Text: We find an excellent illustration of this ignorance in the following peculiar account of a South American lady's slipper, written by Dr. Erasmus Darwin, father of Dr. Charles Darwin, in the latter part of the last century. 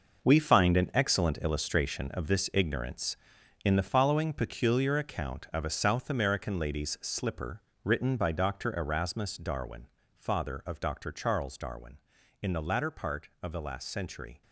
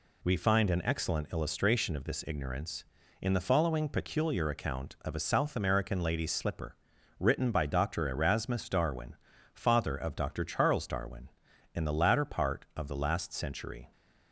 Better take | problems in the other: second | gets quieter; strong; throughout; 10.5 dB

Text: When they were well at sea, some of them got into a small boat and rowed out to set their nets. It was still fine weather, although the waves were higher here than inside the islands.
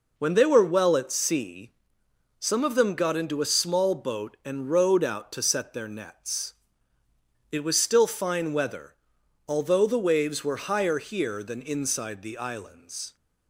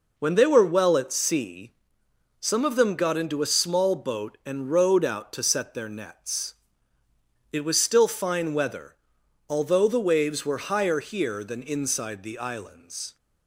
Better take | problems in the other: neither | none

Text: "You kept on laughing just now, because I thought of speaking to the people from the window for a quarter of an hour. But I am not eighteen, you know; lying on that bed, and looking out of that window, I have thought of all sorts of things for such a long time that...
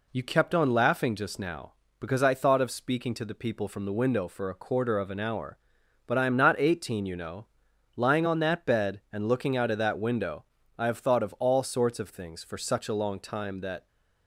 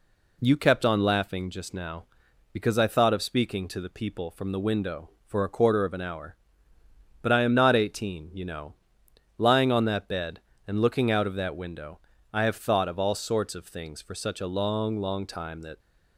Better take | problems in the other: first | says "long" twice; at 15.0 s

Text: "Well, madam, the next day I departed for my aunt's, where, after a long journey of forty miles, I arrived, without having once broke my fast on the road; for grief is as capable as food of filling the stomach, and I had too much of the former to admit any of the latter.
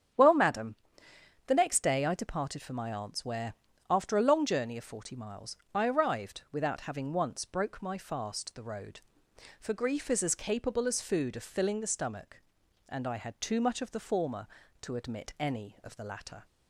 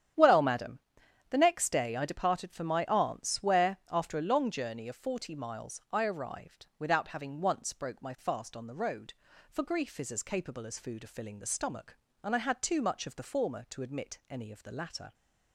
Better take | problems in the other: second | starts louder than the rest; strong; until 1.8 s; 8.5 dB; strong in the second // skips "on"; at 8.5 s

